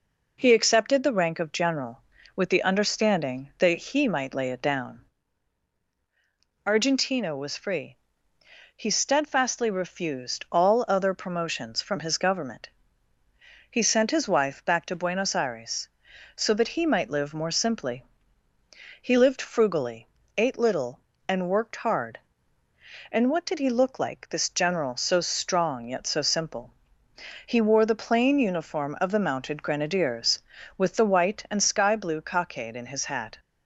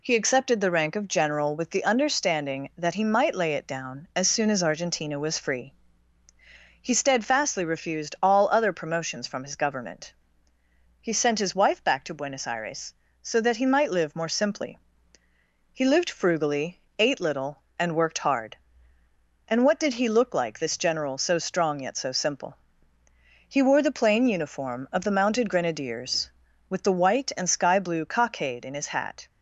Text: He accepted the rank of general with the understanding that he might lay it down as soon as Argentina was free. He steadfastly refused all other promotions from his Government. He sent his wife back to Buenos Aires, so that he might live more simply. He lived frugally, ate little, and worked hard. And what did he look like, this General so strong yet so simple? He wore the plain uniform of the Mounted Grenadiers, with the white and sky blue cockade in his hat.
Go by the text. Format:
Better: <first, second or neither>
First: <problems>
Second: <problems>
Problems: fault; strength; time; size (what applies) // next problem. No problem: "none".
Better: second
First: skips "as soon as"; at 5.8 s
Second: none